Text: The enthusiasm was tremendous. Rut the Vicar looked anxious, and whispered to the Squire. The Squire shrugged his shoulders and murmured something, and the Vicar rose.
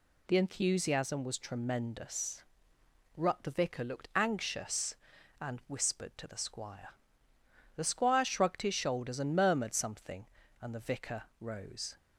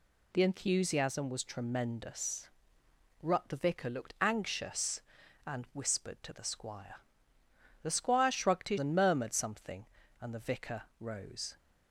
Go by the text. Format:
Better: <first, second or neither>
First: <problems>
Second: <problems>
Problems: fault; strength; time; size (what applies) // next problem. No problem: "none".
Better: first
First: pauses between "Vicar" and "rose"; slight; at 11.2 s; 0.18 s long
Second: skips "shoulders"; at 8.7 s // pauses between "Vicar" and "rose"; slight; at 10.8 s; 0.18 s long